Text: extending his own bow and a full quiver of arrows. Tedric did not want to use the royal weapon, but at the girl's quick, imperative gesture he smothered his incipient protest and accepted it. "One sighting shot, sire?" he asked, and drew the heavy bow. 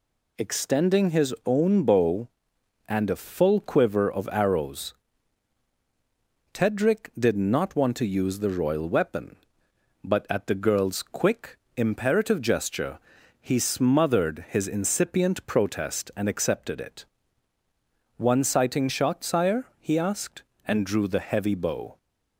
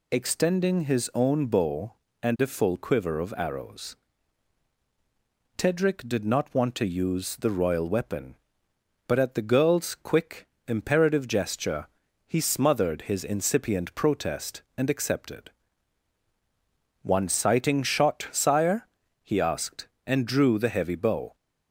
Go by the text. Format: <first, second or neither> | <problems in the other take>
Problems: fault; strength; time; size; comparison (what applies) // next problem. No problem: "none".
first | pauses between "gesture" and "he"; at 11.8 s; 0.40 s long; also in the first // skips "it"; at 16.2 s